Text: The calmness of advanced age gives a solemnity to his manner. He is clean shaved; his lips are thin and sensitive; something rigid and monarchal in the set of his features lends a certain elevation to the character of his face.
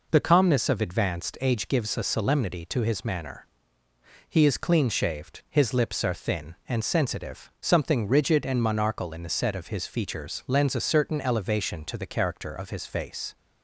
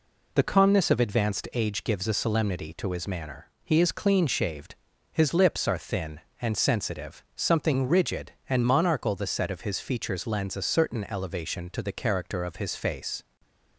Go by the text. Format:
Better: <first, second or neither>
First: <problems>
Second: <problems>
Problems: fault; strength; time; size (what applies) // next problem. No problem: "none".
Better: first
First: none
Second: skips "in"; at 9.1 s